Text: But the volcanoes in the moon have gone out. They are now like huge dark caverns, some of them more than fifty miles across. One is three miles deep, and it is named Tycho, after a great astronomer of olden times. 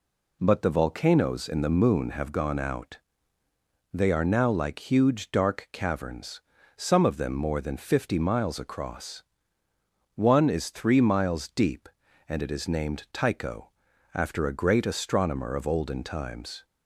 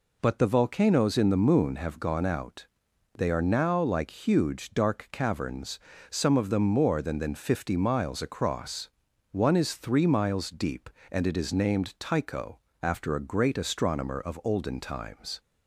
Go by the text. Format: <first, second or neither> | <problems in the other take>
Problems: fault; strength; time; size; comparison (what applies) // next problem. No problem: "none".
first | says "than" twice; at 7.1 s